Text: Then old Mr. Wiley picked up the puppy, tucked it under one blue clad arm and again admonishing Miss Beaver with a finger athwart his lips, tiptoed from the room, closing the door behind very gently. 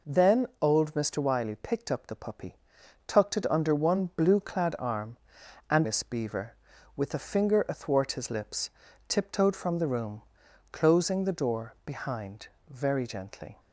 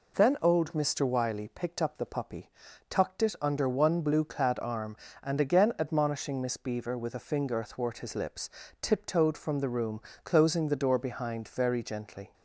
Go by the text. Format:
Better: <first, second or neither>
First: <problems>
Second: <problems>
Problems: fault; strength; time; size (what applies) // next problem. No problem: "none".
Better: second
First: pauses between "Then" and "old"; slight; at 0.4 s; 0.16 s long // skips "again admonishing"; at 5.8 s // pauses between "behind" and "very"; slight; at 12.4 s; 0.20 s long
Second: none